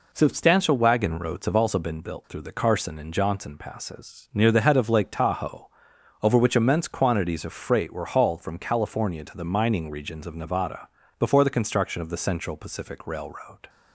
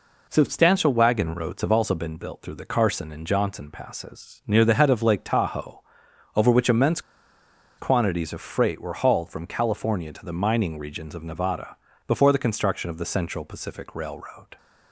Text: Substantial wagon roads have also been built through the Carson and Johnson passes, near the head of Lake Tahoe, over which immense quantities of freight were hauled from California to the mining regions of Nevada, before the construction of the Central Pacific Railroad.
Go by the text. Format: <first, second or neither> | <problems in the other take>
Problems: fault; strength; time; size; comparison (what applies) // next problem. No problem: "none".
first | pauses between "immense" and "quantities"; noticeable; at 6.9 s; 0.78 s long